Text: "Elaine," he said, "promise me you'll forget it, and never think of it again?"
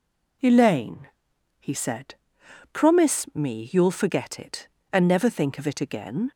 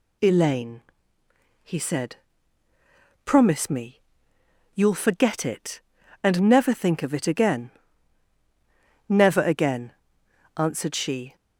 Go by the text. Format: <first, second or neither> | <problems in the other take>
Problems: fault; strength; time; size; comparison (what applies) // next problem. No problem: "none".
first | pauses between "me" and "you'll"; noticeable; at 4.0 s; 0.74 s long // goes on to say "Never again answered she"; strong; from 9.0 s on; 2.2 s long